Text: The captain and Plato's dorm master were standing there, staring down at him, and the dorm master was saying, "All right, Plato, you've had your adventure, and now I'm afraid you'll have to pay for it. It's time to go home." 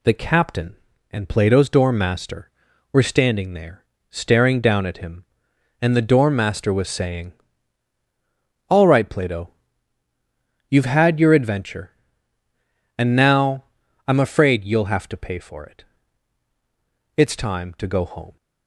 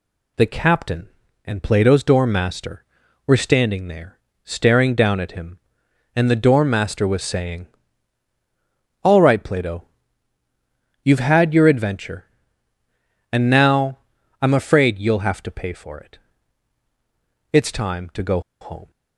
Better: first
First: pauses between "now" and "I'm"; at 13.6 s; 0.42 s long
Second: pauses between "now" and "I'm"; at 13.9 s; 0.42 s long // pauses between "go" and "home"; slight; at 18.3 s; 0.21 s long

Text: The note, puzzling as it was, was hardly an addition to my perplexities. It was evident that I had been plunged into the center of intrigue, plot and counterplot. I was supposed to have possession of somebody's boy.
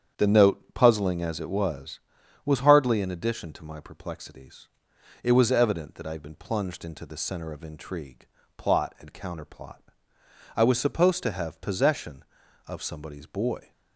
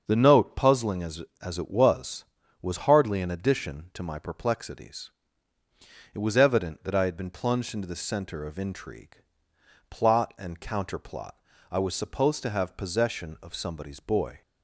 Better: first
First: starts louder than the rest; strong; until 1.3 s; 8 dB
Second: starts louder than the rest; until 1.0 s; 6.5 dB // says "as" twice; at 1.4 s

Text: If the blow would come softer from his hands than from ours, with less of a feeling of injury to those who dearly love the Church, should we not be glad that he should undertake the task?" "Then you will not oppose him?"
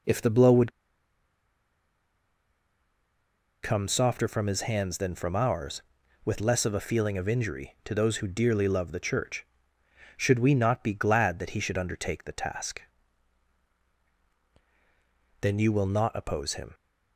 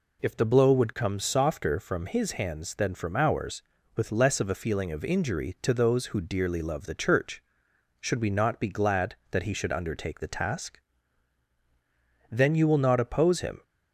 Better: second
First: pauses between "would" and "come"; strong; at 0.7 s; 2.9 s long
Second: none

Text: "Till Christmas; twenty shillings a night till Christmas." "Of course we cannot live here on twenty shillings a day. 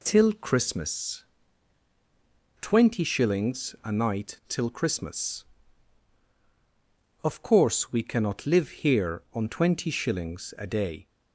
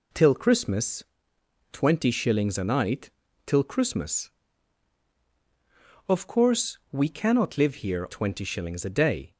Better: first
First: none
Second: pauses between "night" and "till"; slight; at 3.1 s; 0.34 s long // skips "on"; at 8.0 s

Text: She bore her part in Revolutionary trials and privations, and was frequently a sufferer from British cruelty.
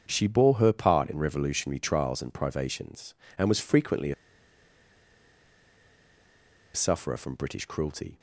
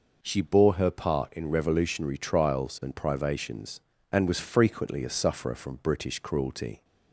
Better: second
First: starts louder than the rest; until 1.1 s; 7 dB // pauses between "a" and "sufferer"; strong; at 4.1 s; 2.6 s long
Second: none

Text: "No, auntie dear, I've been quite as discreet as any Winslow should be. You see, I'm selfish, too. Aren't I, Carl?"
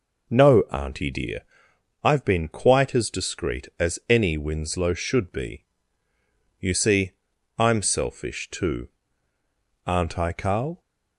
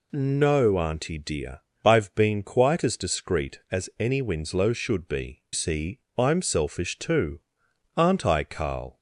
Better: first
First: none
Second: skips "You"; at 5.4 s

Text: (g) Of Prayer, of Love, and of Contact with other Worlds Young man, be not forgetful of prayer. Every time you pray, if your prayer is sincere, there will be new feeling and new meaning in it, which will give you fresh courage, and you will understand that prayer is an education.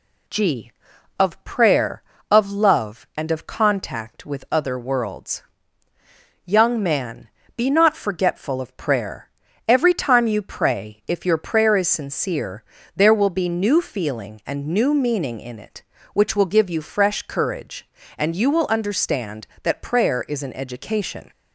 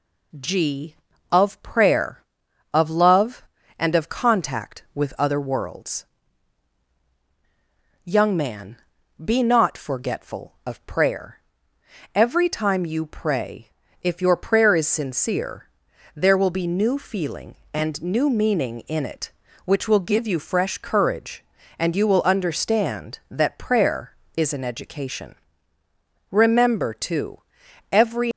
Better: first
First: pauses between "Worlds" and "Young"; at 5.4 s; 1.0 s long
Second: pauses between "Worlds" and "Young"; strong; at 6.0 s; 2.0 s long // goes on to say "Remember too every"; strong; from 26.2 s on; 2.0 s long

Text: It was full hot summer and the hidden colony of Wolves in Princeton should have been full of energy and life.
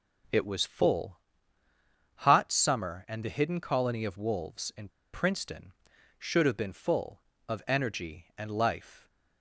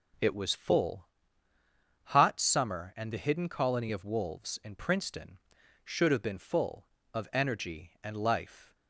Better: second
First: pauses between "full" and "hot"; noticeable; at 1.1 s; 0.96 s long // pauses between "in" and "Princeton"; slight; at 4.8 s; 0.24 s long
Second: pauses between "full" and "hot"; noticeable; at 1.0 s; 0.96 s long

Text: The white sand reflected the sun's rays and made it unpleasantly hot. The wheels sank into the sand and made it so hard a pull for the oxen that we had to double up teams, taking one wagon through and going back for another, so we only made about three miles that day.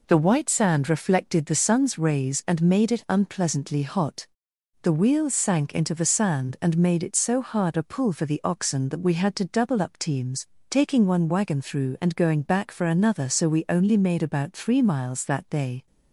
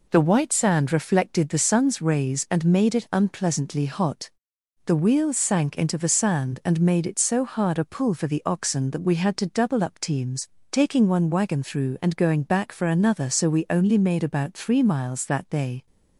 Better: neither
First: none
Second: none

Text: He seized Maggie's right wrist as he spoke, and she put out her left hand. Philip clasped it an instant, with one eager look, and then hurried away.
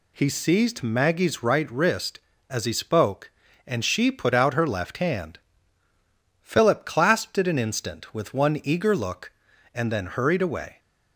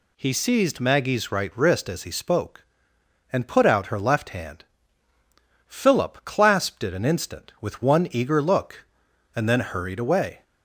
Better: first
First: none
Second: skips "she"; at 3.4 s

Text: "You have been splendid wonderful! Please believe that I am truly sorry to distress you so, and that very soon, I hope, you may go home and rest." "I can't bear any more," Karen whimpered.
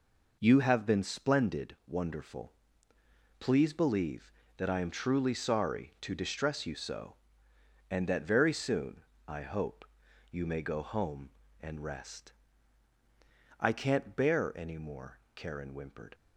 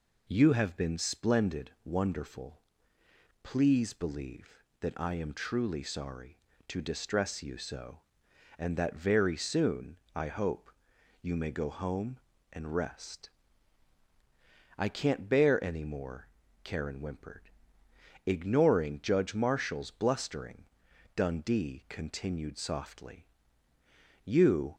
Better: first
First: none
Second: goes on to say "Ignoring Judge Marshall's blustering Dundee continued softly You"; strong; from 18.2 s on; 6.5 s long

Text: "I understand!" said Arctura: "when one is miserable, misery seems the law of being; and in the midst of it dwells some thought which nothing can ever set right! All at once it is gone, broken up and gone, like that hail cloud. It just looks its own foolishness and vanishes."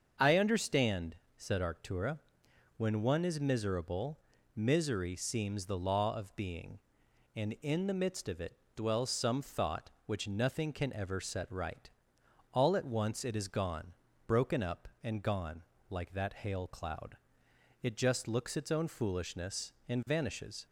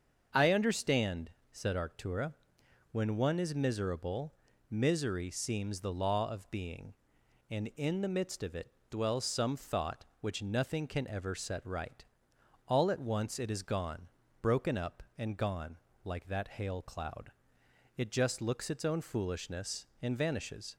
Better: neither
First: starts louder than the rest; until 1.4 s; 6.5 dB // pauses between "it" and "dwells"; slight; at 8.5 s; 0.20 s long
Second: starts louder than the rest; until 1.5 s; 6.5 dB // pauses between "it" and "dwells"; slight; at 8.6 s; 0.20 s long

